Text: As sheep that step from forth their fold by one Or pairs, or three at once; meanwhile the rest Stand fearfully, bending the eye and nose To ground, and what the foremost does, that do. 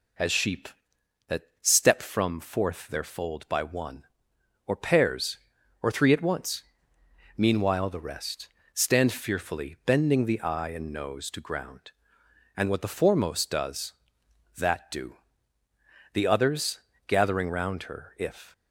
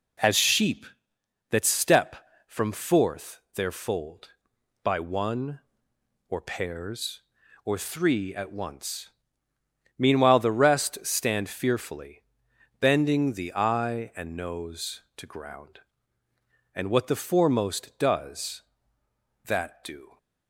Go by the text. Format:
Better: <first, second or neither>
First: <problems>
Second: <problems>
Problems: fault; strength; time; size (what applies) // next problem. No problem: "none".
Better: second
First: pauses between "that" and "step"; slight; at 1.4 s; 0.18 s long // pauses between "rest" and "Stand"; slight; at 8.4 s; 0.24 s long // goes on to say "The others gathering round her if"; strong; from 16.1 s on; 2.4 s long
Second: none